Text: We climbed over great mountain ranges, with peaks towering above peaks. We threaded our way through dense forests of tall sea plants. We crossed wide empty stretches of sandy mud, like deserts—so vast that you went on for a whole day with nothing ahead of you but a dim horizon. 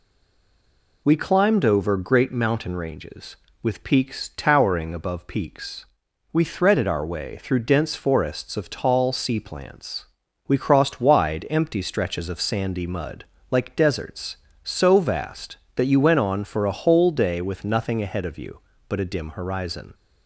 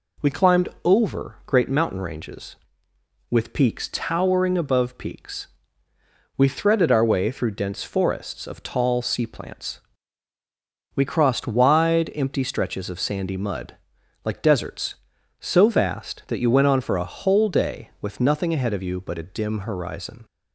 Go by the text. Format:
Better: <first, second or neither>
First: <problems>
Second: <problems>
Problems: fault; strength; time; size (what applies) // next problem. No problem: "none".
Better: second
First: stays silent before the first word; until 1.0 s; 1.0 s long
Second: none